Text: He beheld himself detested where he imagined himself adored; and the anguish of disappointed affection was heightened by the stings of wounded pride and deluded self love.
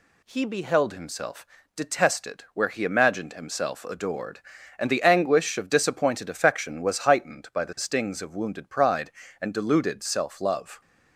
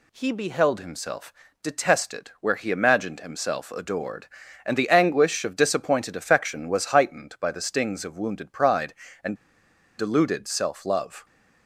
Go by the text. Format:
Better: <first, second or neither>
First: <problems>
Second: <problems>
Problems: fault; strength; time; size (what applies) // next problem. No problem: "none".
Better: first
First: pauses between "himself" and "detested"; slight; at 1.4 s; 0.30 s long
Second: pauses between "himself" and "detested"; slight; at 1.3 s; 0.30 s long // pauses between "and" and "deluded"; noticeable; at 9.3 s; 0.62 s long